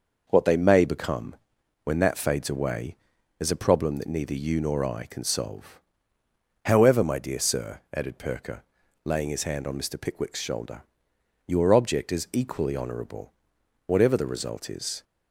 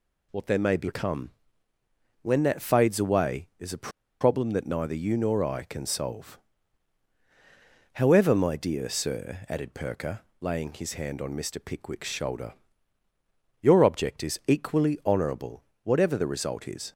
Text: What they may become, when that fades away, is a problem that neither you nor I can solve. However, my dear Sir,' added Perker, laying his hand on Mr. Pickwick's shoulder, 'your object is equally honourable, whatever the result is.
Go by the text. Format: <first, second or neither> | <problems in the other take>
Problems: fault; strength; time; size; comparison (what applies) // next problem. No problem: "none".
first | pauses between "a" and "problem"; slight; at 3.8 s; 0.32 s long